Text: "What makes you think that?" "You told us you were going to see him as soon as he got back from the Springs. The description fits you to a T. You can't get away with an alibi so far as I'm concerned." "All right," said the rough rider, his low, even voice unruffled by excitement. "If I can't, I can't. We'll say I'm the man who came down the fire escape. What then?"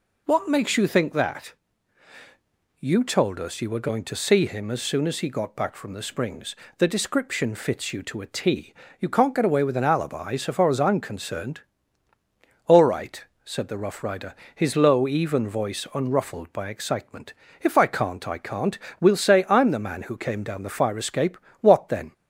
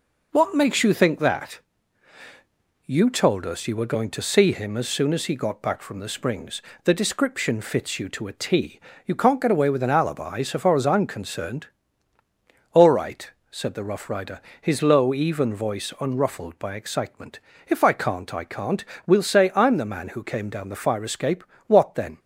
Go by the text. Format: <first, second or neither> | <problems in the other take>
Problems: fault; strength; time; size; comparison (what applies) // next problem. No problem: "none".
first | gets quieter; noticeable; throughout; 4 dB